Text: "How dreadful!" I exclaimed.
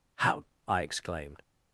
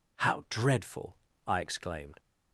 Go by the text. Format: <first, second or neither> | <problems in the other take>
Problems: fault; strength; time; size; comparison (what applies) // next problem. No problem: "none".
second | skips "dreadful"; at 0.5 s